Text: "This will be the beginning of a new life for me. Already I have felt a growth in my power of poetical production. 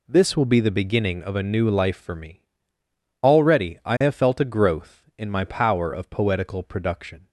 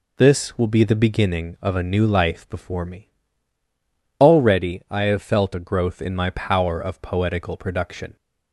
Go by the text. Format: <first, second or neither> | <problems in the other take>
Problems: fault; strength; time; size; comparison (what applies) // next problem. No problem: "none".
first | says "before" for "for"; at 2.5 s